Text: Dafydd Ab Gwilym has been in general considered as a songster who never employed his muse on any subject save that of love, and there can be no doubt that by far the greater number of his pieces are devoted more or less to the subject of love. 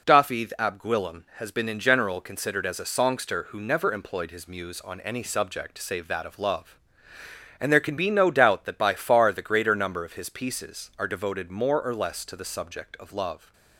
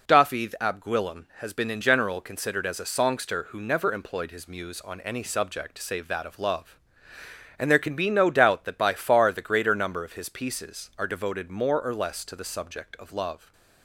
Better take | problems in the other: neither | none

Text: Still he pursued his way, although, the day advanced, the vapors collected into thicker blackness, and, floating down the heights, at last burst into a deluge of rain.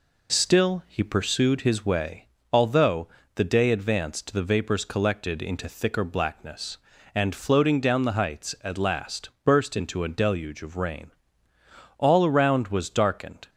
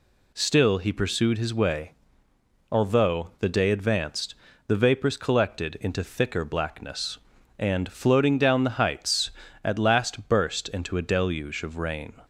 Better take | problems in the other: second | goes on to say "All around was darkened"; from 11.9 s on; 1.5 s long

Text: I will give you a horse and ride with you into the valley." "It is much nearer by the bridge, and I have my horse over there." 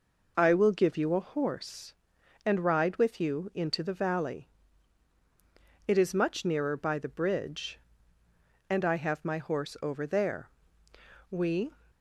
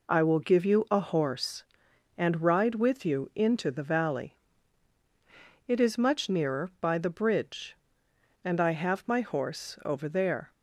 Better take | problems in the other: second | goes on to say "We"; slight; from 11.2 s on; 0.44 s long

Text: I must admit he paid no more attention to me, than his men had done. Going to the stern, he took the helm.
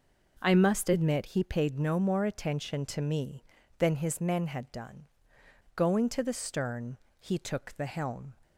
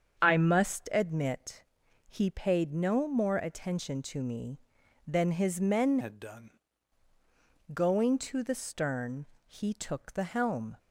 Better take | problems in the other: first | starts louder than the rest; strong; until 1.2 s; 7.5 dB // pauses between "admit" and "he"; at 1.6 s; 0.44 s long // changes voice from "had" to "done"; from 6.0 to 6.5 s; 0.5 s long

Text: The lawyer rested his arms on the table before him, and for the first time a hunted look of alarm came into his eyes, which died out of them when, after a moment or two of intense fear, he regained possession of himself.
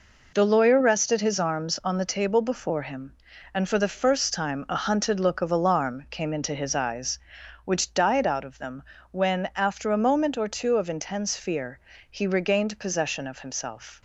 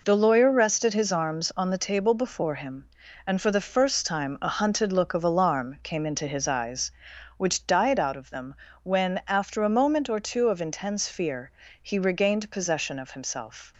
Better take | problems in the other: neither | pauses between "them" and "when"; slight; the same in both

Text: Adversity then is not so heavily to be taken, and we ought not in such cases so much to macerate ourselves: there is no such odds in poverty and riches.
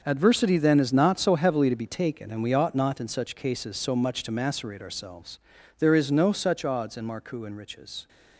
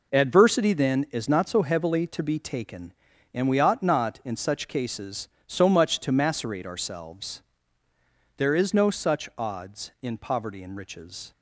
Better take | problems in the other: second | starts louder than the rest; noticeable; until 1.0 s; 6 dB // says "marcou" for "poverty"; at 7.0 s

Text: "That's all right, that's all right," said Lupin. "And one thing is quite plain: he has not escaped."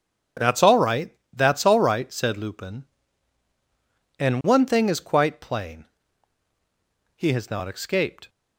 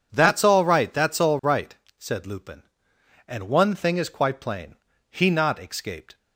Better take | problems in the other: first | skips "has"; at 5.3 s

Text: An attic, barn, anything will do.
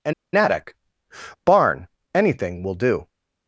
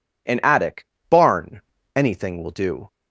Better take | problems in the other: second | pauses between "An" and "attic"; slight; at 0.1 s; 0.22 s long

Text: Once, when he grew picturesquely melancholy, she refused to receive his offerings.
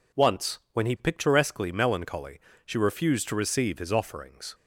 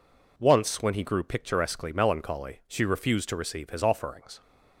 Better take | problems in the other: second | skips "grew"; at 0.9 s

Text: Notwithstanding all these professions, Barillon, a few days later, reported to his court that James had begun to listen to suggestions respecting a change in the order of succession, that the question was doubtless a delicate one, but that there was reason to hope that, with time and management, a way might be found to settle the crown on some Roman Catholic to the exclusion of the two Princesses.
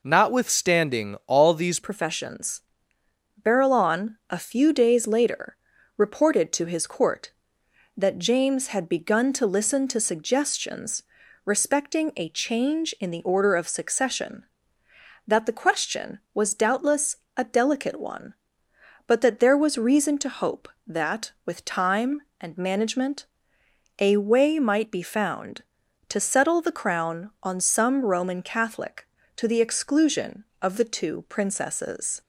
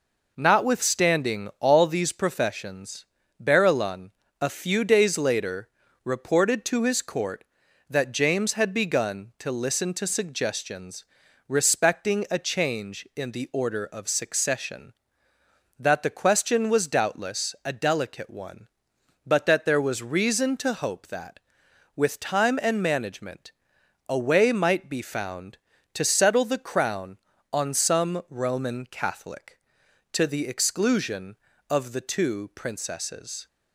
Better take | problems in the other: second | changes voice at "professions"; from 1.7 s on; 30.5 s long // pauses between "suggestions" and "respecting"; at 11.0 s; 0.42 s long; also in the second // pauses between "doubtless" and "a"; slight; at 17.1 s; 0.20 s long

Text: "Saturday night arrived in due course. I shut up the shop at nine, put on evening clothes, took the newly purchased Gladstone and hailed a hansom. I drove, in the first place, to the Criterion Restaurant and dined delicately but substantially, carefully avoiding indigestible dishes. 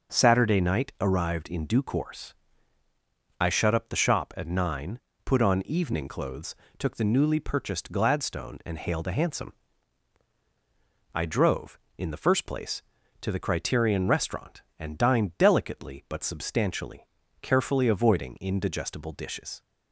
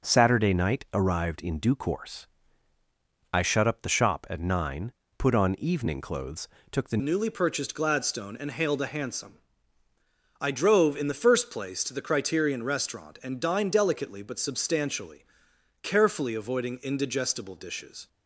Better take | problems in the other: first | changes voice at "newly"; from 7.0 s on; 11.0 s long

